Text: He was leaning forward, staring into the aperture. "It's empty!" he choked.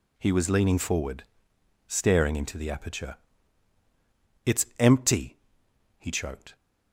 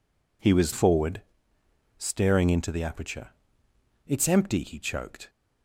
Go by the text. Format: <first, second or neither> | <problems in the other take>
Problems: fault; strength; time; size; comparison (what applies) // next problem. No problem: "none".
first | skips "leaning"; at 0.7 s